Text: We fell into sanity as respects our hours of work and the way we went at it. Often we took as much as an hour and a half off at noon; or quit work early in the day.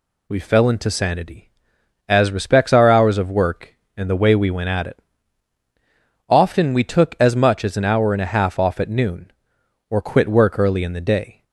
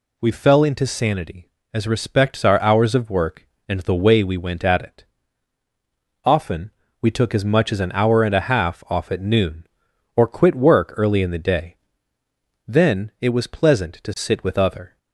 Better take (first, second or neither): first